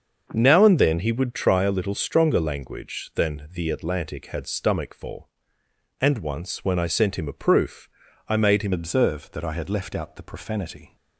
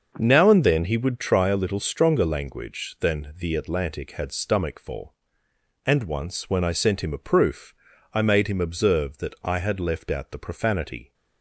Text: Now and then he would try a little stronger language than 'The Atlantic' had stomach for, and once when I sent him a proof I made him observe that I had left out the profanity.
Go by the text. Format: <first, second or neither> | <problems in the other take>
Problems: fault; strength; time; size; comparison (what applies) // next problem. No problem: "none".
second | starts louder than the rest; until 1.3 s; 6.5 dB; also in the second // pauses between "proof" and "I"; at 7.8 s; 0.40 s long; also in the second // changes voice at "observe"; from 8.7 s on; 2.2 s long